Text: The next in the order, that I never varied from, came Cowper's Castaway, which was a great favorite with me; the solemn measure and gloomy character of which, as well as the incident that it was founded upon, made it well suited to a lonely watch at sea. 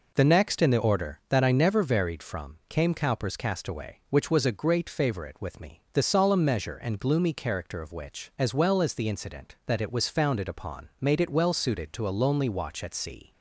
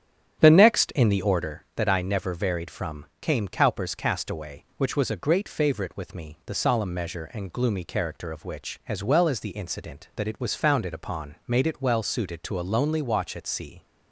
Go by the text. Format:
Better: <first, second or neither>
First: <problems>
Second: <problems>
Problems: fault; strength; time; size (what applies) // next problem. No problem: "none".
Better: first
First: none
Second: starts louder than the rest; strong; until 1.5 s; 9.5 dB